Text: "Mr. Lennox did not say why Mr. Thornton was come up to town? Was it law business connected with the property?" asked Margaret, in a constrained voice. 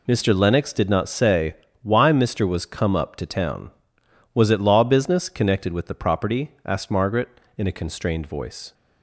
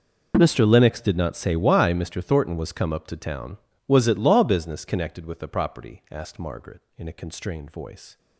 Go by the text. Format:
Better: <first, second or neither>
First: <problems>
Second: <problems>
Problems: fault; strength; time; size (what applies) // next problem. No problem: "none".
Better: second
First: pauses between "say" and "why"; slight; at 1.5 s; 0.26 s long // skips "Thornton"; at 2.4 s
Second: none